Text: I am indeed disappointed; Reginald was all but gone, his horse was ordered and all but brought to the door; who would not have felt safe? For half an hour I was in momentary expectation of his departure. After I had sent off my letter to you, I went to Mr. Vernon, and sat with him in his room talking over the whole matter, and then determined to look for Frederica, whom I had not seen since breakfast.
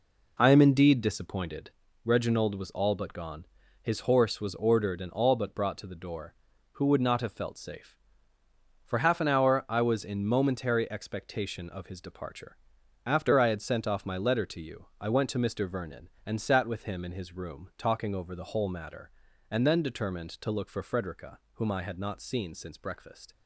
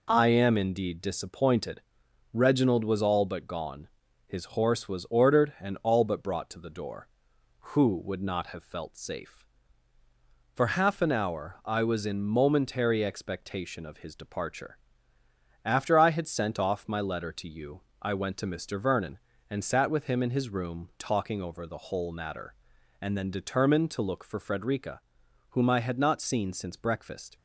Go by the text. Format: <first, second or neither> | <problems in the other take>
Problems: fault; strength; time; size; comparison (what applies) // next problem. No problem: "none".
neither | none